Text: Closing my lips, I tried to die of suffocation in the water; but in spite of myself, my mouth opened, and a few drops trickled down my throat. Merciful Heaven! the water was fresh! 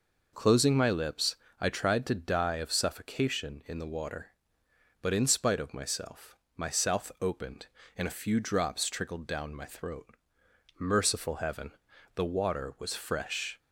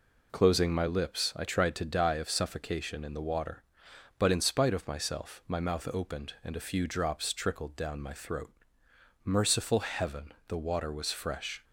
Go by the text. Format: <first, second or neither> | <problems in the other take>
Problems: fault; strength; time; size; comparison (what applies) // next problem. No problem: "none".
second | says "south" for "mouth"; at 6.7 s